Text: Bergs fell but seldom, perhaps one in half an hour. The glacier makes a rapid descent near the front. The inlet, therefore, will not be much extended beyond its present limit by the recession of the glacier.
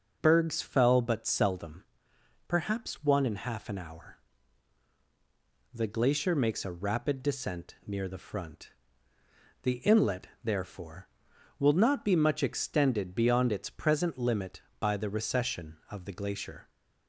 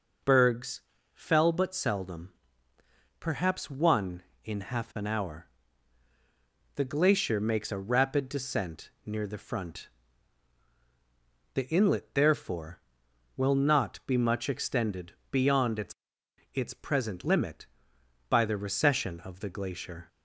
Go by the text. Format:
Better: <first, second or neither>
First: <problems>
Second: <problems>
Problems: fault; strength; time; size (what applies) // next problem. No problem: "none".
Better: first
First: none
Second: pauses between "Bergs" and "fell"; slight; at 0.8 s; 0.34 s long // pauses between "descent" and "near"; slight; at 8.8 s; 0.16 s long // pauses between "extended" and "beyond"; slight; at 15.1 s; 0.18 s long // says "its" twice; at 16.5 s